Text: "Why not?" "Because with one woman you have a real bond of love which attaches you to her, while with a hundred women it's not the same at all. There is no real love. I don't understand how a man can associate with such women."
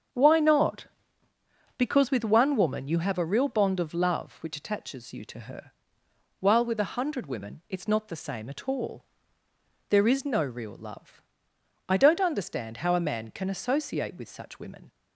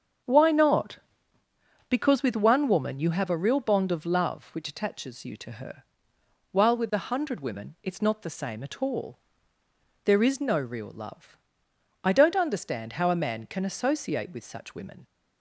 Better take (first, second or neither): neither